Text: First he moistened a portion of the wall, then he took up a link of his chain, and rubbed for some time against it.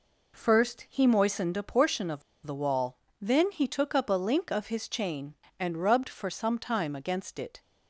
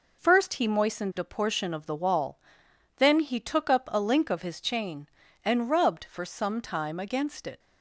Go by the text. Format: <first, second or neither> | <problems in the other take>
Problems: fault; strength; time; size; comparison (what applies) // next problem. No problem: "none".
second | pauses between "of" and "the"; slight; at 2.2 s; 0.24 s long